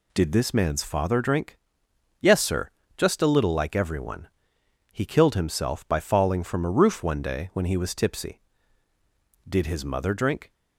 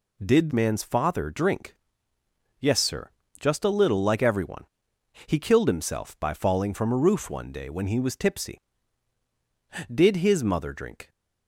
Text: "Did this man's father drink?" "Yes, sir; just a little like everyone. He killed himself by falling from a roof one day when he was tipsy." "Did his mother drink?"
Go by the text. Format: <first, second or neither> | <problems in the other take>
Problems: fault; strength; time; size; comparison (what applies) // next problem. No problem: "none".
first | skips "this"; at 0.5 s